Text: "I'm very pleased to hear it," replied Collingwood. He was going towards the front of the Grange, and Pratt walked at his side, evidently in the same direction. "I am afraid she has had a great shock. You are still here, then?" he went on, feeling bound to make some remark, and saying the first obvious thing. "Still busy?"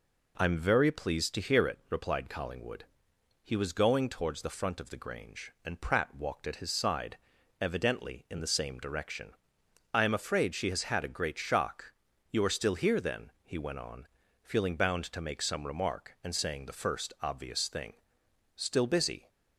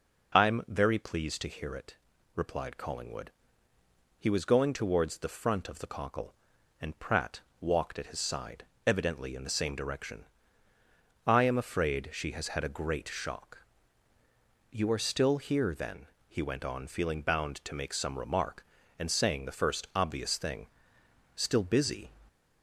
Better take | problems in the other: first | says "Cockle" for "Grange"; at 5.8 s // pauses between "Pratt" and "walked"; slight; at 7.4 s; 0.18 s long

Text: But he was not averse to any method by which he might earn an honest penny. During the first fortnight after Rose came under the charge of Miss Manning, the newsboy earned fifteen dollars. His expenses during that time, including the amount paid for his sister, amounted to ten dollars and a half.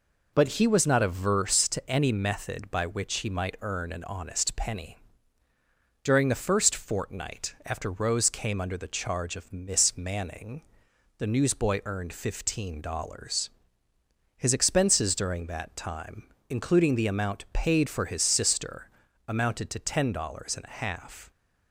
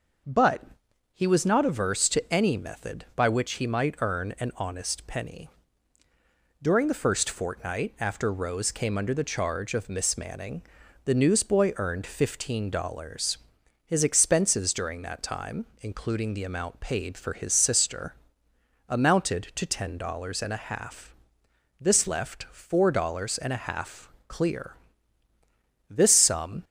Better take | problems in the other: first | pauses between "But" and "he"; noticeable; at 0.6 s; 0.52 s long // goes on to say "This left four dollars and a half clear This sum"; strong; from 21.7 s on; 4.8 s long

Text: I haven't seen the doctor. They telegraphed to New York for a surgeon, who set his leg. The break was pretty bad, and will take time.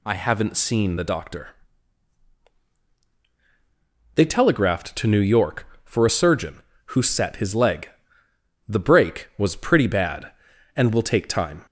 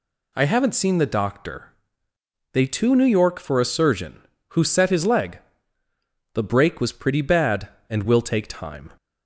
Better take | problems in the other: first | skips "telegraphed"; at 2.6 s

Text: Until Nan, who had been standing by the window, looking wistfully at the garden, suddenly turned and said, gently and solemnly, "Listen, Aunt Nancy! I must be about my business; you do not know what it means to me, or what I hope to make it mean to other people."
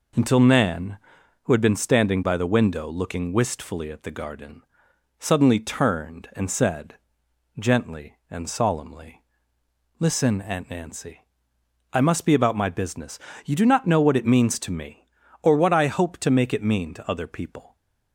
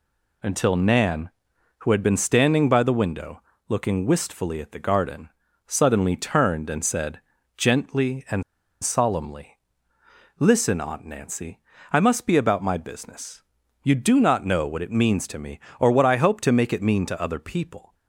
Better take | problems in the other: first | pauses between "and" and "solemnly"; at 8.4 s; 0.40 s long

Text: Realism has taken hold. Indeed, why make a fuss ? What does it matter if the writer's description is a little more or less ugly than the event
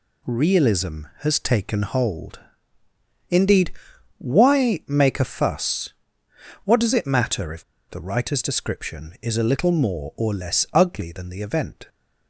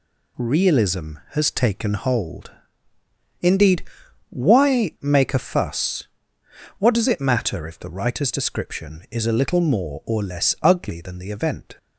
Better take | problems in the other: second | pauses between "if" and "the"; slight; at 7.6 s; 0.26 s long

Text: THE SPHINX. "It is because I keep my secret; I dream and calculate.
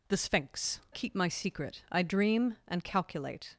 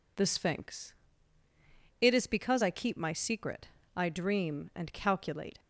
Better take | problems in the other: second | skips "It is because I"; at 0.8 s

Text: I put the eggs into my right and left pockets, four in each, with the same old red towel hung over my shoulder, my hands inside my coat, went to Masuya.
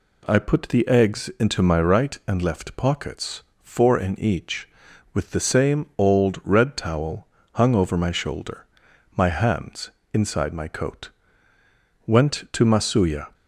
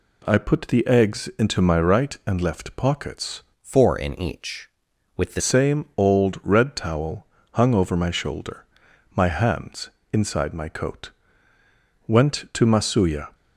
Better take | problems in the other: first | changes voice from "four" to "the"; from 3.6 to 5.4 s; 1.8 s long // pauses between "towel" and "hung"; slight; at 7.2 s; 0.26 s long; slight in the first // pauses between "hands" and "inside"; slight; at 9.9 s; 0.22 s long; slight in the first

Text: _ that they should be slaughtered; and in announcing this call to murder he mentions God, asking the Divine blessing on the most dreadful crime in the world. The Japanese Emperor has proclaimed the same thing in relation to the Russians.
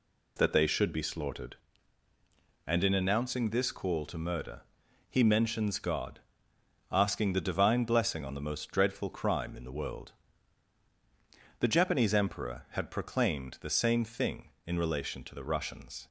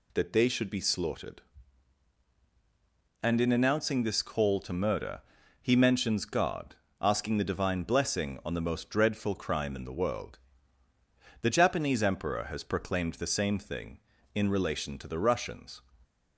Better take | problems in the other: second | pauses between "murder" and "he"; noticeable; at 4.6 s; 0.48 s long; also in the second // says "had" for "has"; at 12.7 s

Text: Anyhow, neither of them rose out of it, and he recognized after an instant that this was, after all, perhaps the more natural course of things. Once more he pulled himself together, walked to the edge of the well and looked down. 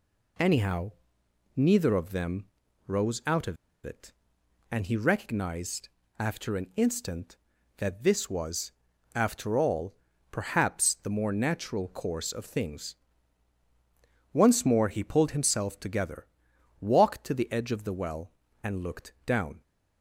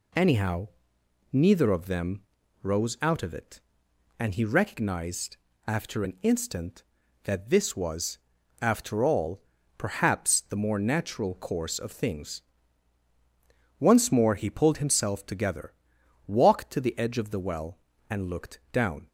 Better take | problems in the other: second | pauses between "them" and "rose"; at 2.4 s; 0.40 s long; also in the second // pauses between "of" and "it"; slight; at 3.5 s; 0.29 s long // pauses between "recognized" and "after"; slight; at 5.8 s; 0.32 s long; slight in the second

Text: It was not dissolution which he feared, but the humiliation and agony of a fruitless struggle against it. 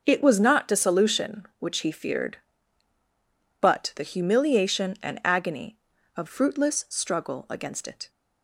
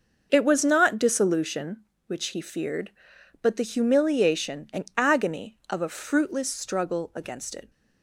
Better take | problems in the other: second | starts louder than the rest; until 1.0 s; 6.5 dB; also in the second // skips "a"; at 6.2 s

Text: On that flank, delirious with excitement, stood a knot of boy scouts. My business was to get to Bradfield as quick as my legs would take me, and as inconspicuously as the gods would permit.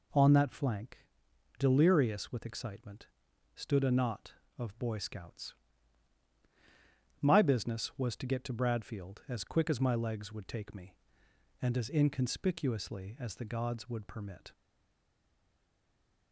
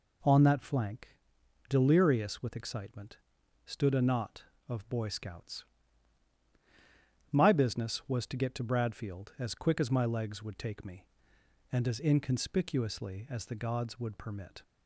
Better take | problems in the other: second | stays silent after the last word; noticeable; from 14.5 s on; 1.8 s long

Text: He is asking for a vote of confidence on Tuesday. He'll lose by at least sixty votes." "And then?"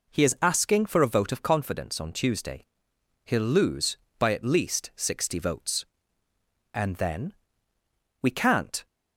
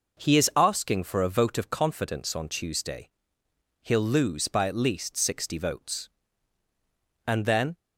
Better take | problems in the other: second | goes on to say "We can't"; noticeable; from 8.2 s on; 0.64 s long

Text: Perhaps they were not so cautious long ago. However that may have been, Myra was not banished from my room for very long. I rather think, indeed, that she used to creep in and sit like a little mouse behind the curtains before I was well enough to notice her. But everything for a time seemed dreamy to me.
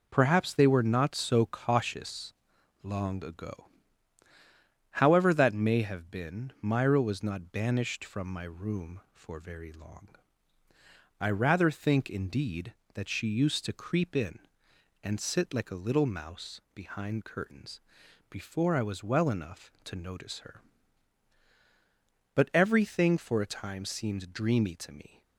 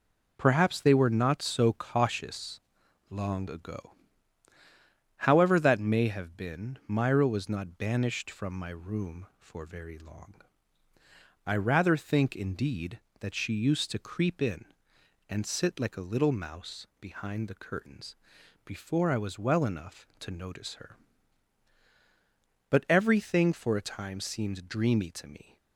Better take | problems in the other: second | pauses between "cautious" and "long"; noticeable; at 2.3 s; 0.50 s long; noticeable in the second // skips "the"; at 17.2 s // pauses between "curtains" and "before"; noticeable; at 17.8 s; 0.48 s long; noticeable in the second

